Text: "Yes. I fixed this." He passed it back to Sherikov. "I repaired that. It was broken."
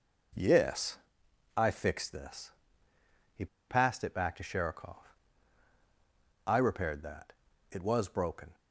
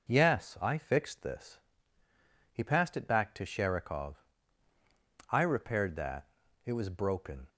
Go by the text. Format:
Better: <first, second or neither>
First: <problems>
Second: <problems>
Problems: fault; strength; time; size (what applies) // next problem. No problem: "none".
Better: second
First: pauses between "He" and "passed"; slight; at 3.4 s; 0.23 s long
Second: none